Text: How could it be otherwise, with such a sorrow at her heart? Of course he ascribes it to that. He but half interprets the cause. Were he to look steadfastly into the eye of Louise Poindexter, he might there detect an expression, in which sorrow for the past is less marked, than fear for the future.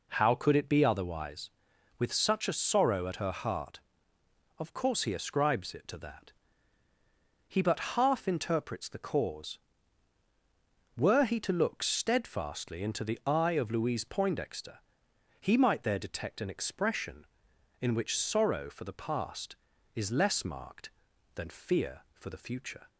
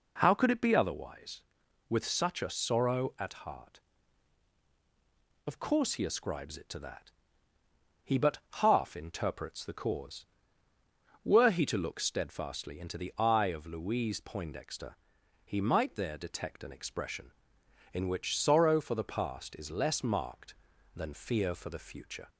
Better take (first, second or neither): first